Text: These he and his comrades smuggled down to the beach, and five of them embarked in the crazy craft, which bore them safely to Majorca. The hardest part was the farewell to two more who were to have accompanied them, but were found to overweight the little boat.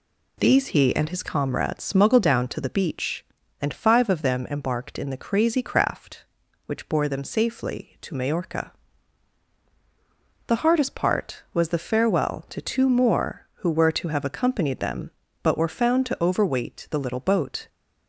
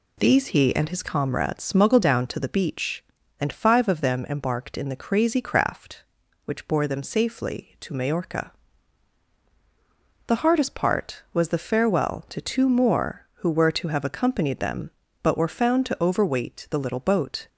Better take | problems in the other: neither | none

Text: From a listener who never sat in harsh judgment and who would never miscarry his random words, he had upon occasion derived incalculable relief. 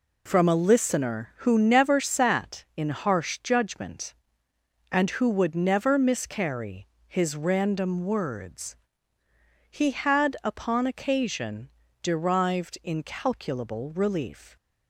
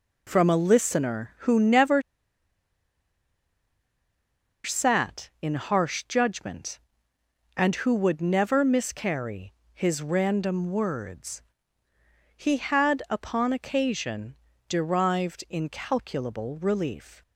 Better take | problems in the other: first | pauses between "never" and "sat"; strong; at 2.0 s; 2.6 s long // pauses between "miscarry" and "his"; slight; at 9.5 s; 0.20 s long; slight in the first // pauses between "occasion" and "derived"; slight; at 14.3 s; 0.34 s long; slight in the first

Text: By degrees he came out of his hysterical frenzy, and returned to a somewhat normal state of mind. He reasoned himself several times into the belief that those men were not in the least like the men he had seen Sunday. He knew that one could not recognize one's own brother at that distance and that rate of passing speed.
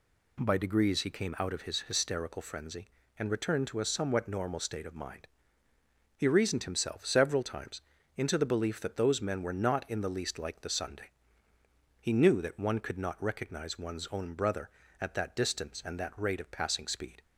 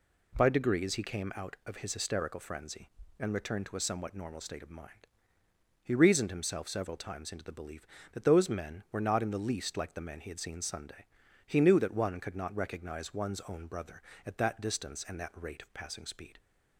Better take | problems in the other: second | pauses between "times" and "into"; slight; at 7.8 s; 0.36 s long // skips "men he had seen"; at 10.6 s

